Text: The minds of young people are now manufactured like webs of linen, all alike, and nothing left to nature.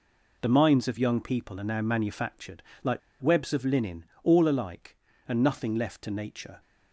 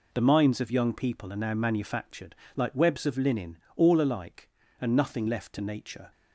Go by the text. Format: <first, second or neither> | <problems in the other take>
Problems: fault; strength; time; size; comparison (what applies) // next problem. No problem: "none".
second | pauses between "manufactured" and "like"; slight; at 2.6 s; 0.22 s long; slight in the second // pauses between "like" and "webs"; slight; at 2.9 s; 0.22 s long